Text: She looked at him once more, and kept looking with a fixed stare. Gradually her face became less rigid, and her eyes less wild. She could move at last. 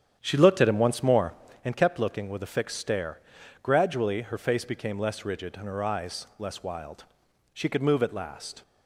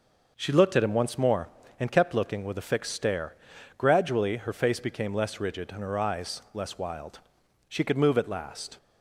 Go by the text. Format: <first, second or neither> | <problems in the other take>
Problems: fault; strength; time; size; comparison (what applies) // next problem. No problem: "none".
second | starts louder than the rest; strong; until 1.6 s; 9.5 dB